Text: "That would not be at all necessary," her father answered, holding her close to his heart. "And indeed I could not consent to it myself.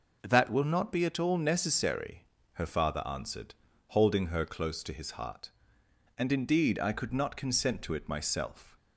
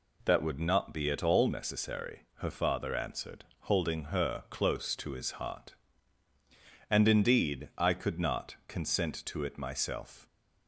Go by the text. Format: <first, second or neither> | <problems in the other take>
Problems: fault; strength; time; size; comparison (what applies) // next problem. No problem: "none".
second | says "will" for "would"; at 0.5 s